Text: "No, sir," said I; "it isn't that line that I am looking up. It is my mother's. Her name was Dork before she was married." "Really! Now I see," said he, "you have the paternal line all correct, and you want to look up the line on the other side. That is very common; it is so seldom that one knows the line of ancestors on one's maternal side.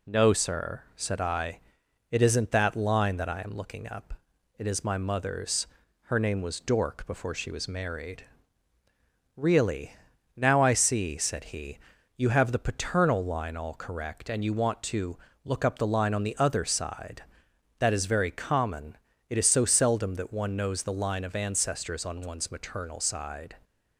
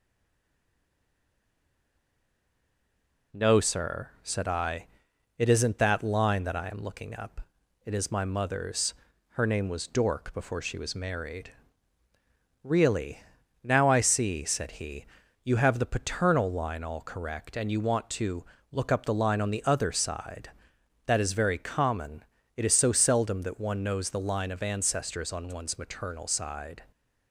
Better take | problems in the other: first | stays silent before the first word; strong; until 3.3 s; 3.3 s long // pauses between "to" and "look"; slight; at 18.4 s; 0.30 s long; slight in the first

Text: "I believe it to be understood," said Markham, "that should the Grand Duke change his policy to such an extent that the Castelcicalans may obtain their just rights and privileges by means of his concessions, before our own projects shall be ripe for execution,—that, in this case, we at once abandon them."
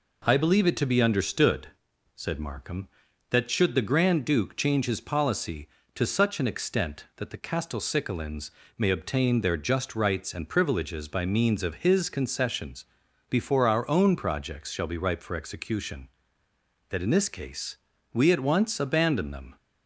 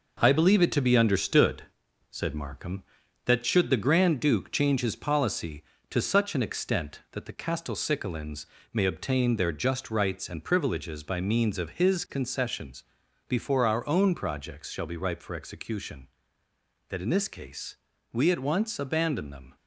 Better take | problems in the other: first | gets quieter; throughout; 6.5 dB // pauses between "Castelcicalans" and "may"; slight; at 8.4 s; 0.28 s long; slight in the first

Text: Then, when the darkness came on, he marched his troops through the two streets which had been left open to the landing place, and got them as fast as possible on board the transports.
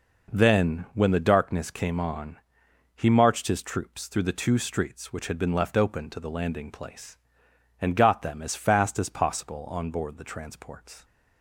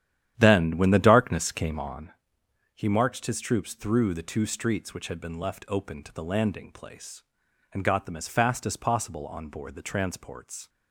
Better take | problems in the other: first | starts louder than the rest; strong; until 2.1 s; 10.5 dB

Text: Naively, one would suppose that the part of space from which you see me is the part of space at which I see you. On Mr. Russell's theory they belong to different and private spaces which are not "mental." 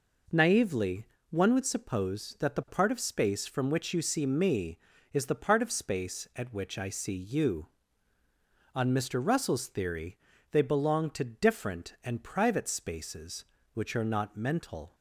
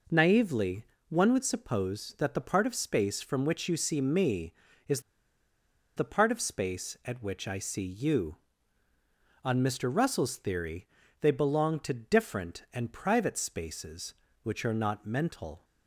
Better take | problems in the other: first | pauses between "is" and "the"; noticeable; at 4.9 s; 0.96 s long // pauses between "theory" and "they"; slight; at 10.8 s; 0.36 s long; slight in the first

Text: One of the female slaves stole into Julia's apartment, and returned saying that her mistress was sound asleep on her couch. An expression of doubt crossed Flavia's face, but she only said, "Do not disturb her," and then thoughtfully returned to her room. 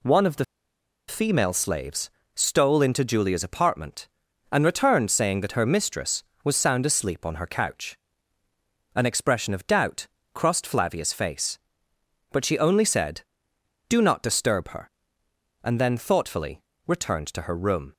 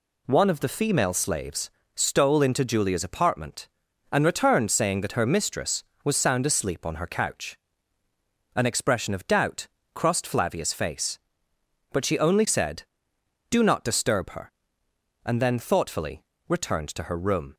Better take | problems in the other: second | pauses between "the" and "female"; noticeable; at 0.4 s; 0.63 s long // pauses between "slaves" and "stole"; slight; at 2.0 s; 0.26 s long; slight in the second // pauses between "doubt" and "crossed"; slight; at 10.0 s; 0.26 s long; slight in the second // pauses between "thoughtfully" and "returned"; slight; at 16.6 s; 0.24 s long; slight in the second

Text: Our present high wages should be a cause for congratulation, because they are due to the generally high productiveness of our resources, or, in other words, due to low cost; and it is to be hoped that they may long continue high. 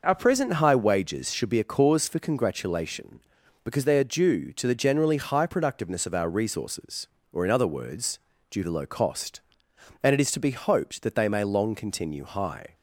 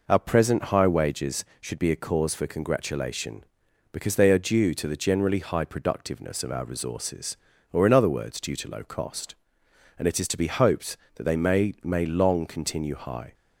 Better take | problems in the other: first | says "may" twice; at 11.8 s

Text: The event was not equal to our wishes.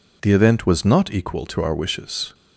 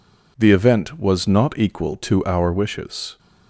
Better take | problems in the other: neither | none

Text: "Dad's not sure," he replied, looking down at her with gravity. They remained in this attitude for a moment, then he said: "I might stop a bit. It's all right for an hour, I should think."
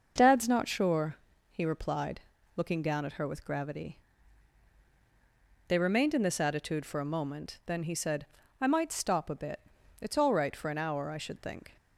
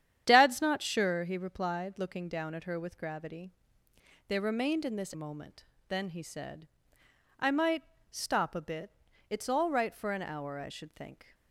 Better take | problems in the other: first | starts louder than the rest; strong; until 1.2 s; 9.5 dB; noticeable in the first // skips "attitude for a"; at 5.1 s // pauses between "might" and "stop"; slight; at 7.8 s; 0.30 s long

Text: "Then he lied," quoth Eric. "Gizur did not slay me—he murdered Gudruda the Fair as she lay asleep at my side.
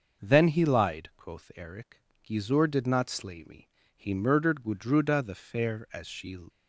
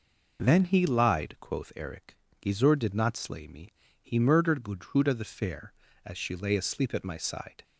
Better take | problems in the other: second | stops before "lay asleep at my side"; at 6.4 s

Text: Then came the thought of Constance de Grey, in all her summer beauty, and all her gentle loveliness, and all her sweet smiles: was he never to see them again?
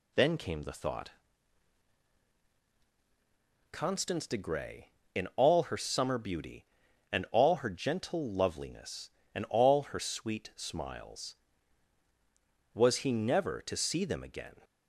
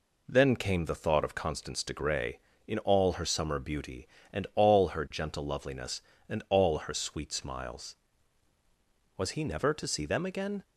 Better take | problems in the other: second | skips "of"; at 2.4 s

